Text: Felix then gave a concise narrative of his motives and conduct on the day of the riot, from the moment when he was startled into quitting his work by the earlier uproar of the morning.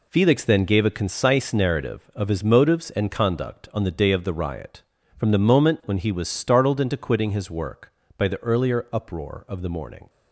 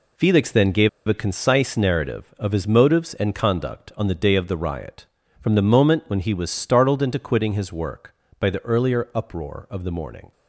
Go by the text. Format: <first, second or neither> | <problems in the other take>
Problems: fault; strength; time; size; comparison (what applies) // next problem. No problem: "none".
first | pauses between "gave" and "a"; slight; at 0.8 s; 0.19 s long